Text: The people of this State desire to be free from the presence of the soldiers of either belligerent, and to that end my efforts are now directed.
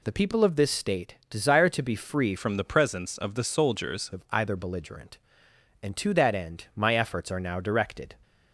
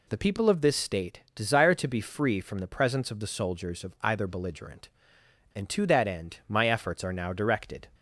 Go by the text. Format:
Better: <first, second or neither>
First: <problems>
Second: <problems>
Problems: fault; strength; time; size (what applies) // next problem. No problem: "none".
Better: second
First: changes voice from "from" to "soldiers"; from 2.3 to 4.1 s; 1.8 s long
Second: none